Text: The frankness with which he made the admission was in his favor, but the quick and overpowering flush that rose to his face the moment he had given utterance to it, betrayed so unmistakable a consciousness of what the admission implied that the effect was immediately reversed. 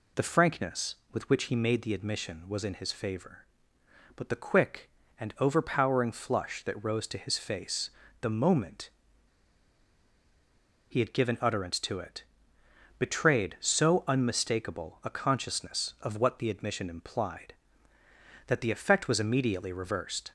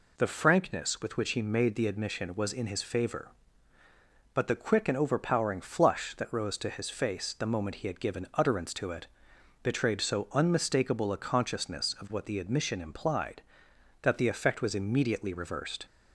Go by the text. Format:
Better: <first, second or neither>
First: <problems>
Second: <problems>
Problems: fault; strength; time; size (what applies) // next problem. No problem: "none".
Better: second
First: pauses between "face" and "the"; slight; at 7.9 s; 0.30 s long // pauses between "moment" and "he"; strong; at 8.9 s; 1.9 s long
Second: none